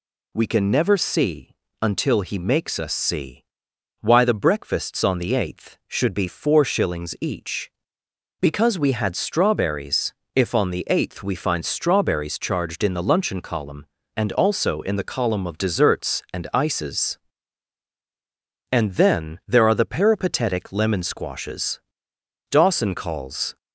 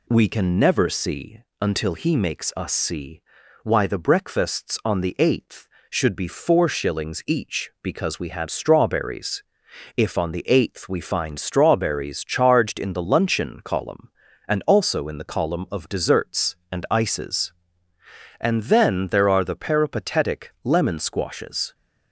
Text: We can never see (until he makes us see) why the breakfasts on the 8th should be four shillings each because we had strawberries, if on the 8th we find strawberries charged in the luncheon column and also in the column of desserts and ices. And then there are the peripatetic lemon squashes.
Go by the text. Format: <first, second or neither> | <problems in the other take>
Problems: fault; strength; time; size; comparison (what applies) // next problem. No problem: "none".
second | goes on to say "Dawson calls"; noticeable; from 22.5 s on; 1.0 s long